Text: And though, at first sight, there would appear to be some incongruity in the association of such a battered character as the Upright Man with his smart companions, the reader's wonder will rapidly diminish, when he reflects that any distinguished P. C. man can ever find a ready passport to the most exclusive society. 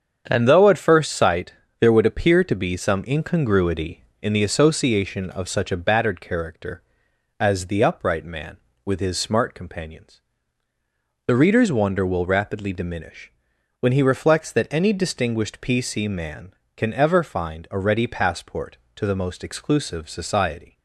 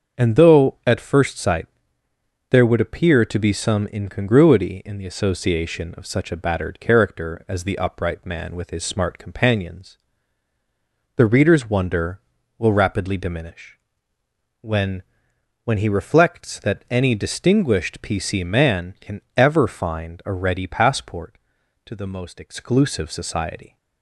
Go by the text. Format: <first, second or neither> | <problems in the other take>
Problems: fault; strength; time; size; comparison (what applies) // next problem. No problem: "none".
first | starts louder than the rest; until 1.2 s; 7 dB; strong in the first // says "when" twice; at 15.6 s // pauses between "can" and "ever"; slight; at 19.2 s; 0.16 s long